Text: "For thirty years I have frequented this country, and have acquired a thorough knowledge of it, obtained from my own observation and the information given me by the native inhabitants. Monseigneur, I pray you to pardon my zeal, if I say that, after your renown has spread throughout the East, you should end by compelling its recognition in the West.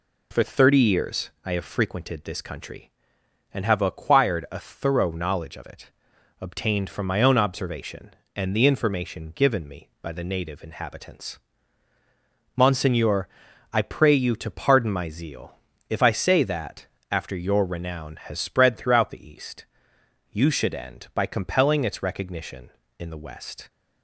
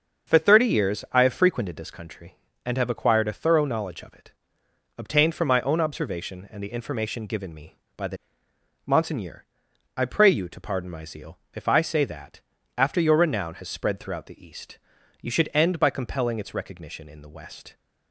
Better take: first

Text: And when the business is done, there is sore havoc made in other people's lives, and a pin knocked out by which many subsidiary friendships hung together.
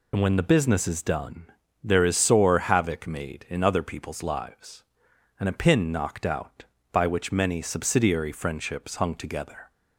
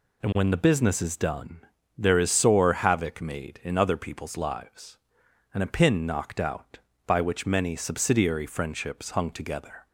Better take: second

